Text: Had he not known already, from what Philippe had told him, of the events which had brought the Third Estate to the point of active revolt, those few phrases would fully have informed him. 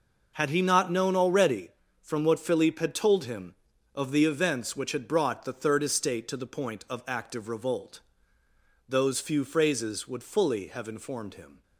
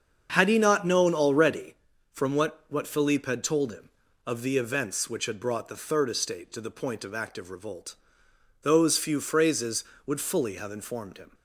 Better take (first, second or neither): first